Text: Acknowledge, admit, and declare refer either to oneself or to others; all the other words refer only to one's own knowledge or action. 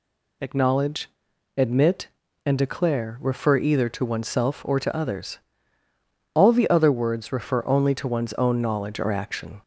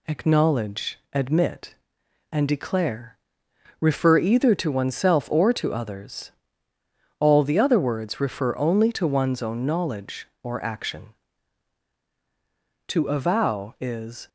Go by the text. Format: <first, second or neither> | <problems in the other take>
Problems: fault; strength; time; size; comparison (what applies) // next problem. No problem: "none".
first | pauses between "declare" and "refer"; noticeable; at 3.1 s; 0.64 s long // goes on to say "To avow is"; from 12.8 s on; 1.4 s long